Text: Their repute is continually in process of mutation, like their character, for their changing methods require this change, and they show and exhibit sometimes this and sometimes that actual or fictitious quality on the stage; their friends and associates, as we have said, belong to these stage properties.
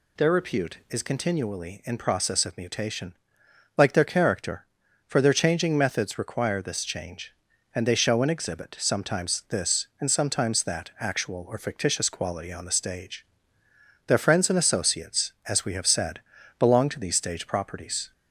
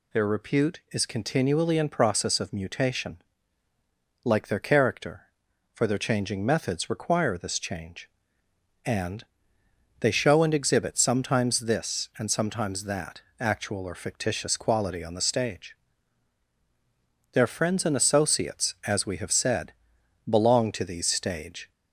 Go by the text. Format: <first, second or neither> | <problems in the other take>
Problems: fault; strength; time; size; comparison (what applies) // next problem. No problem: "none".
first | pauses between "and" and "they"; noticeable; at 9.2 s; 0.78 s long // pauses between "that" and "actual"; slight; at 13.2 s; 0.18 s long // stops before "properties"; at 21.7 s